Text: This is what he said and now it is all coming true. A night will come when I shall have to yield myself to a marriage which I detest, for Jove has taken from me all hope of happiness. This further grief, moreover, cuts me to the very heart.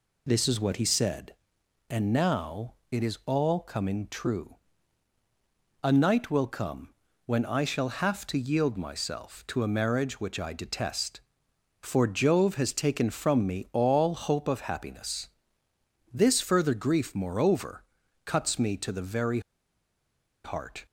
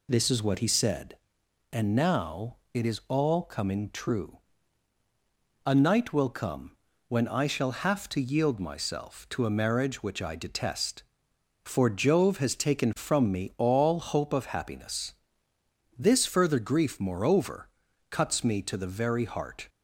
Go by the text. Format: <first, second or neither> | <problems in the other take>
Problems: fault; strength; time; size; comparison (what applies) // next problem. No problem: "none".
second | pauses between "now" and "it"; slight; at 2.7 s; 0.18 s long; slight in the second // pauses between "come" and "when"; slight; at 6.8 s; 0.36 s long; slight in the second // pauses between "very" and "heart"; at 19.3 s; 1.0 s long